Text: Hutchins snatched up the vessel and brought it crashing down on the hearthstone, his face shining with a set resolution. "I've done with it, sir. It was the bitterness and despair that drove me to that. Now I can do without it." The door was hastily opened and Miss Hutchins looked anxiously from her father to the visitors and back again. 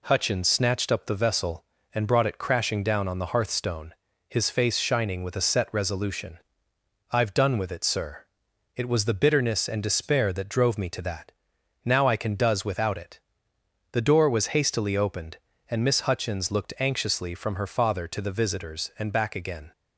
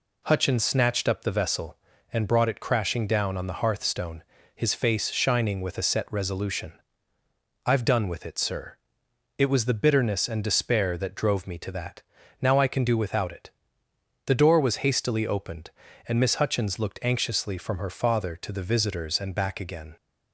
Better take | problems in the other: second | says "does" for "do"; at 12.3 s

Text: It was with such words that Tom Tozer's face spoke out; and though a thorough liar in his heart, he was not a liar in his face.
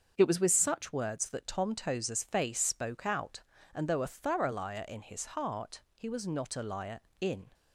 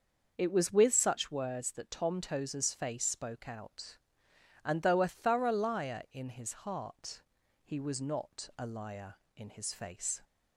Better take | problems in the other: second | starts louder than the rest; until 1.1 s; 6.5 dB; also in the second // stops before "his face"; at 7.5 s

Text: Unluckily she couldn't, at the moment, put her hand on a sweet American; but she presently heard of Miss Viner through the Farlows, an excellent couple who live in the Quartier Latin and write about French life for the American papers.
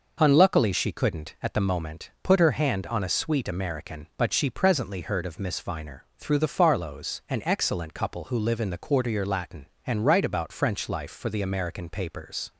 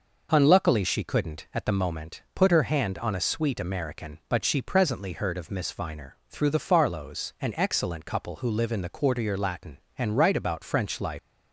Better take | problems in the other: first | stops before "for the American papers"; at 11.1 s

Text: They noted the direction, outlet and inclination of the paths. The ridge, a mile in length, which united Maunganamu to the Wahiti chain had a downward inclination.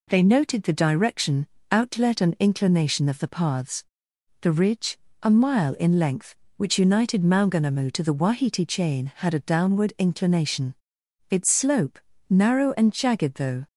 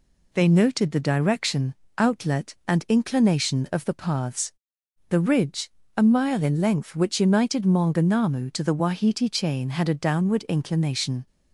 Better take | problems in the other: second | goes on to say "Its slope narrow and jagged though"; strong; from 11.2 s on; 2.3 s long

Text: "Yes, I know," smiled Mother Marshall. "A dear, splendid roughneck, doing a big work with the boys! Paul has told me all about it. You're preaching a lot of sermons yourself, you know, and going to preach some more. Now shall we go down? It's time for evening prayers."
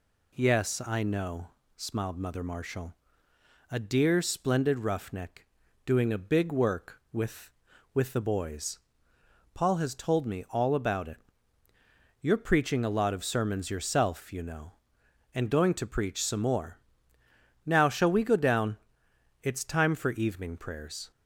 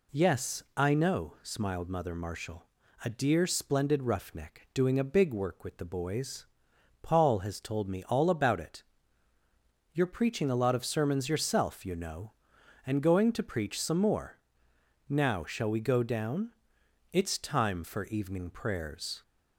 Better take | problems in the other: second | says "with" twice; at 7.9 s

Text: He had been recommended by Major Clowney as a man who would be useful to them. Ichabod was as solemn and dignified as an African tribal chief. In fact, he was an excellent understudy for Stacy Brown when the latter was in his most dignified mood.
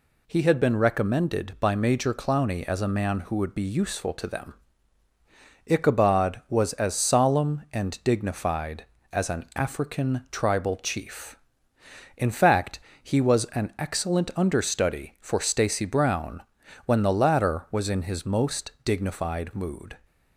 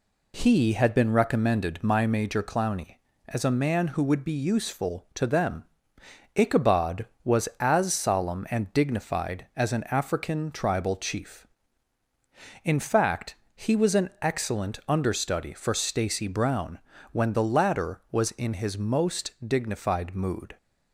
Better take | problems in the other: first | says "my" for "by"; at 1.8 s // pauses between "Brown" and "when"; slight; at 16.7 s; 0.34 s long; also in the first // pauses between "most" and "dignified"; slight; at 19.3 s; 0.16 s long

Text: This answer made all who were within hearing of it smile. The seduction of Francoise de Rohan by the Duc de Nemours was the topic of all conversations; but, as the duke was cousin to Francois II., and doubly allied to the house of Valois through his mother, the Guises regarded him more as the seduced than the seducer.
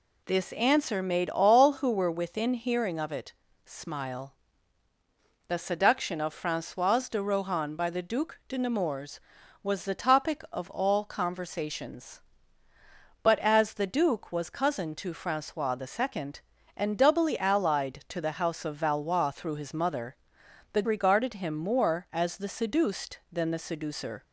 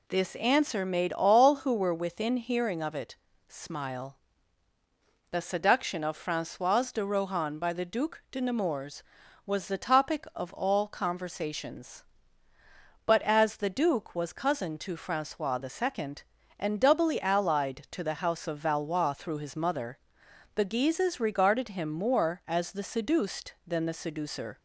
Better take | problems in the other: second | pauses between "it" and "smile"; slight; at 3.3 s; 0.32 s long; slight in the second // skips "Guises"; at 20.8 s

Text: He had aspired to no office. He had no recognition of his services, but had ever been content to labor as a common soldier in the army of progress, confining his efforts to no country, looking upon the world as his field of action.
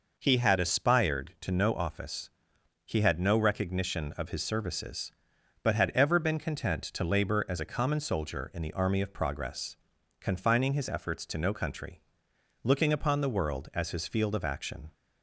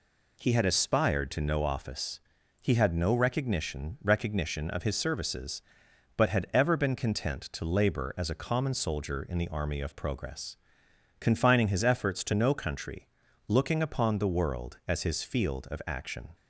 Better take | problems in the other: first | says "recognition" twice; at 4.0 s

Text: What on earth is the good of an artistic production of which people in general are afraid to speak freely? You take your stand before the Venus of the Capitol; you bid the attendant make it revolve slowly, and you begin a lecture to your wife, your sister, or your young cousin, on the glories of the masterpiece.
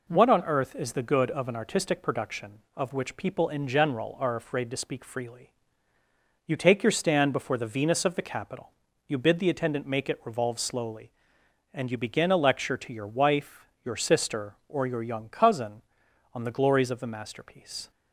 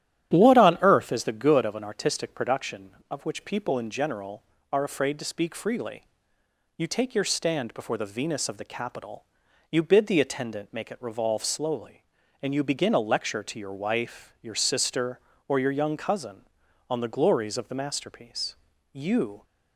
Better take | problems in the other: first | starts louder than the rest; strong; until 1.3 s; 11.5 dB // goes on to say "You"; from 18.9 s on; 0.50 s long

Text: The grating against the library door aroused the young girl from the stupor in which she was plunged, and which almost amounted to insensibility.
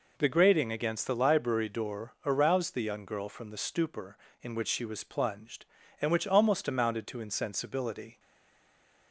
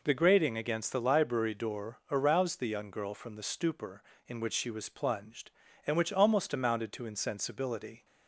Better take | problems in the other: second | stays silent after the last word; slight; from 8.1 s on; 1.0 s long

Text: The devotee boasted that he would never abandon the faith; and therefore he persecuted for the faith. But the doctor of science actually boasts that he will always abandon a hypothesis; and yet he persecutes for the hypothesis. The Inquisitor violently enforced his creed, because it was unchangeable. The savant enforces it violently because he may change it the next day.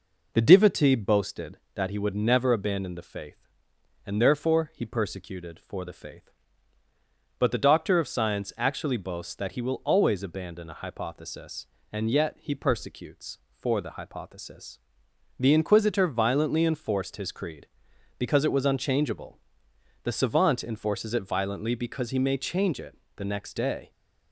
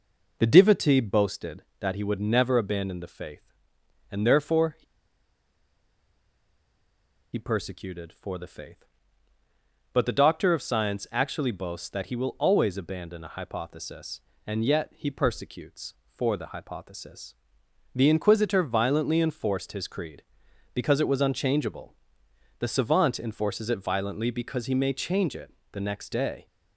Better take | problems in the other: first | pauses between "he" and "persecuted"; strong; at 4.8 s; 2.5 s long // pauses between "it" and "the"; slight; at 25.5 s; 0.20 s long; slight in the first

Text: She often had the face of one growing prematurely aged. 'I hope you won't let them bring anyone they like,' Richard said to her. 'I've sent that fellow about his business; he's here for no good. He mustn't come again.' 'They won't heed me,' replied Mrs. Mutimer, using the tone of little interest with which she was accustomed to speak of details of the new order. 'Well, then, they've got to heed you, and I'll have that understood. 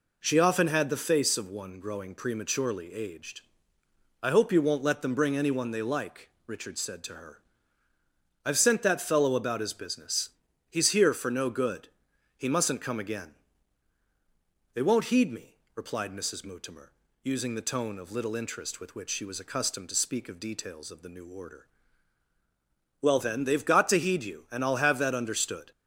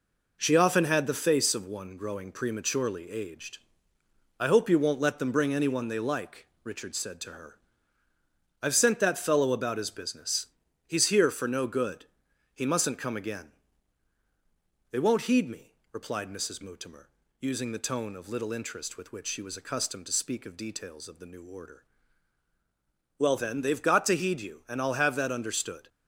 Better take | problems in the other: first | gets quieter; noticeable; throughout; 5.5 dB

